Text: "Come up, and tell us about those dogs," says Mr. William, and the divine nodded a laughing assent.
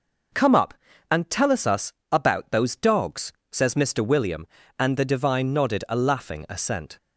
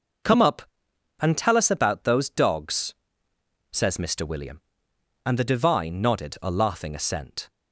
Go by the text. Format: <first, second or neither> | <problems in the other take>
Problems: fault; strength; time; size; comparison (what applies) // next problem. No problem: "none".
second | says "us" twice; at 1.6 s